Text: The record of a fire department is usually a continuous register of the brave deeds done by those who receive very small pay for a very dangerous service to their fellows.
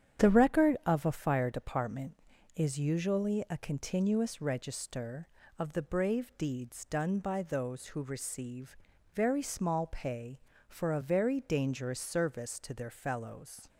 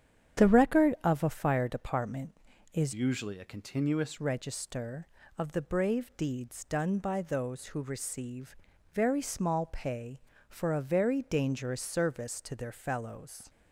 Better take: first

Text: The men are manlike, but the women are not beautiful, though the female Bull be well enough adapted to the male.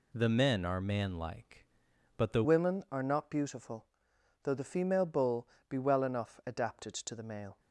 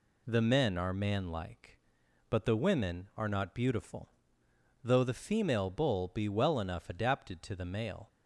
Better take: second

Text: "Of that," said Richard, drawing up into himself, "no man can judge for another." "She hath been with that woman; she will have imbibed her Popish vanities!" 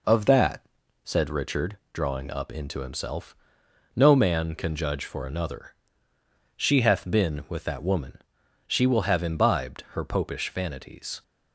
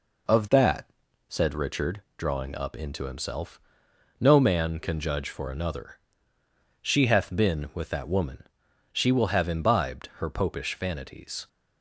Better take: neither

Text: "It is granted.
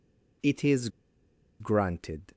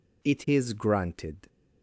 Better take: second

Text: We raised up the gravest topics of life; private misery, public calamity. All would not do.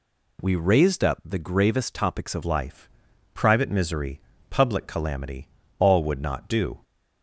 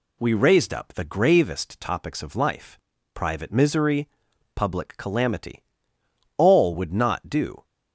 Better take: second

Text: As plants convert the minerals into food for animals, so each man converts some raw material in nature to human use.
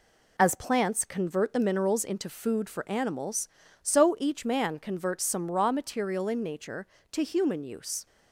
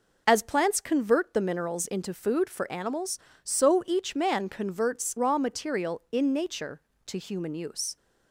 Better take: first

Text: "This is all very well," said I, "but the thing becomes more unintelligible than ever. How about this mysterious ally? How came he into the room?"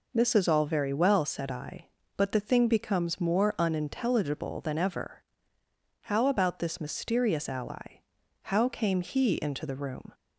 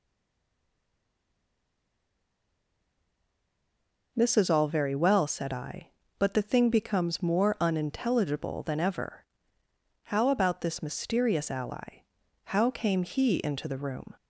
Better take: first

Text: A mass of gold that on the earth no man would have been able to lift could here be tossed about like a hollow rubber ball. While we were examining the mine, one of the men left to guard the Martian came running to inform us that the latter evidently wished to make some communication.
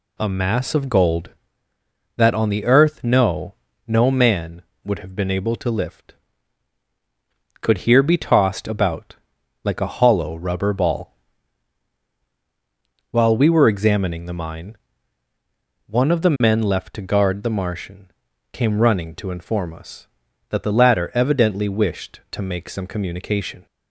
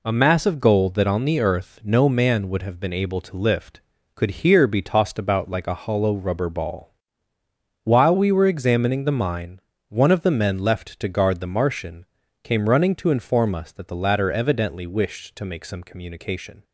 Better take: second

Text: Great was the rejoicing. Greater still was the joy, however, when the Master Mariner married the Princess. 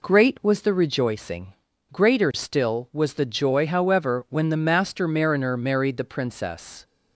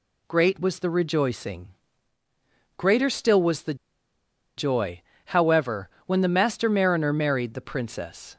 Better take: first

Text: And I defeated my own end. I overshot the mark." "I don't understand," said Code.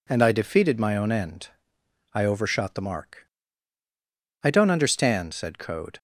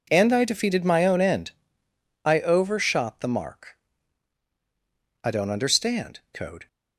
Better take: first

